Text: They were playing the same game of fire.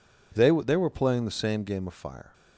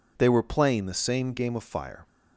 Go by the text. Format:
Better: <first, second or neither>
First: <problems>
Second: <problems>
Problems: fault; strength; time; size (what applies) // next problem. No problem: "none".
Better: second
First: says "They" twice; at 0.5 s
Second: none